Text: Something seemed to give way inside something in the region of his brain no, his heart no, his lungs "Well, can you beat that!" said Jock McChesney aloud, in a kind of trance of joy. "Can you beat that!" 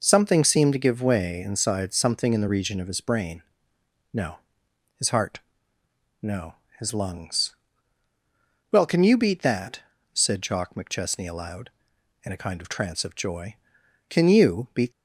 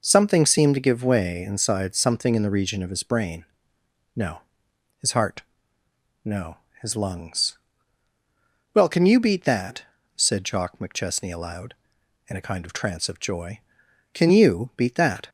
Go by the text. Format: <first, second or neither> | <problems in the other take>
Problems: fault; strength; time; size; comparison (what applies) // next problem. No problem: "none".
second | pauses between "brain" and "no"; noticeable; at 3.4 s; 0.70 s long; noticeable in the second // pauses between "heart" and "no"; noticeable; at 5.4 s; 0.82 s long; noticeable in the second // pauses between "lungs" and "Well"; at 7.5 s; 1.1 s long; also in the second // stops before "that"; at 14.9 s